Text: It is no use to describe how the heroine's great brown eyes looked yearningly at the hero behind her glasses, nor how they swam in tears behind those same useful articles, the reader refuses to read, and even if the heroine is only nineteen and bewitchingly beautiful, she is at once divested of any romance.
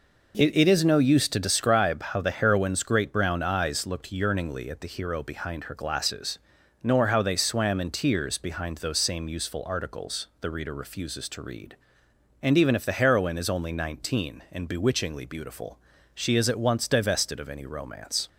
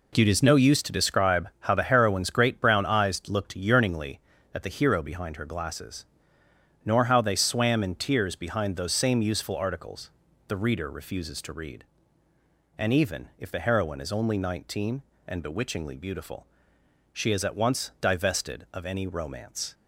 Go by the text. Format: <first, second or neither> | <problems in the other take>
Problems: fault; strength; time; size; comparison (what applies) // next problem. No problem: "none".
second | says "It" twice; at 0.5 s